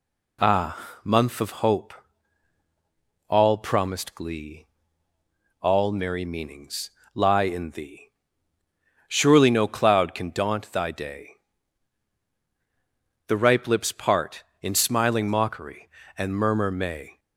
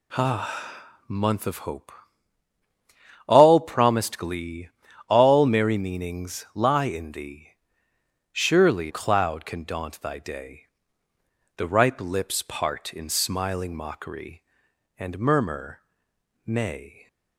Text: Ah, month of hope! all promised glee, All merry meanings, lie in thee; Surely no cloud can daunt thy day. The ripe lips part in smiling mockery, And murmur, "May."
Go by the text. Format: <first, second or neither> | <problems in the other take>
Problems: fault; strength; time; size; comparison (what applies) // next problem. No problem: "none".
first | skips "no"; at 8.9 s